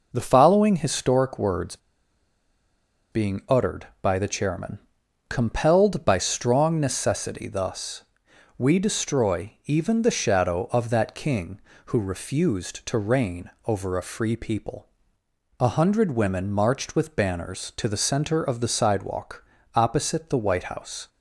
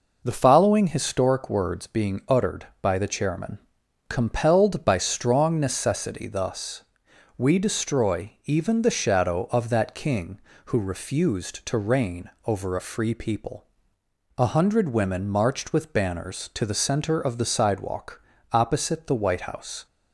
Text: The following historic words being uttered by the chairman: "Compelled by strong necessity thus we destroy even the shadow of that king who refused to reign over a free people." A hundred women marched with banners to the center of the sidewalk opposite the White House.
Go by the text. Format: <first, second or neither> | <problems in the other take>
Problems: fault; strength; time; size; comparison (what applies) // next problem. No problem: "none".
second | pauses between "words" and "being"; strong; at 1.7 s; 1.3 s long // pauses between "thus" and "we"; noticeable; at 8.0 s; 0.52 s long; noticeable in the second // pauses between "reign" and "over"; slight; at 13.5 s; 0.16 s long; slight in the second // pauses between "sidewalk" and "opposite"; slight; at 19.4 s; 0.32 s long; slight in the second